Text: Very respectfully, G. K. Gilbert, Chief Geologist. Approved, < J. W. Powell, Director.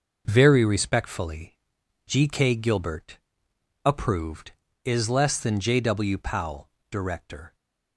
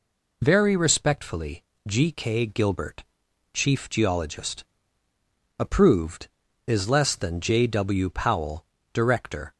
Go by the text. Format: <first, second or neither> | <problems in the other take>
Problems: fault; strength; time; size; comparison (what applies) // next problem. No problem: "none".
second | skips "Chief Geologist"; at 3.5 s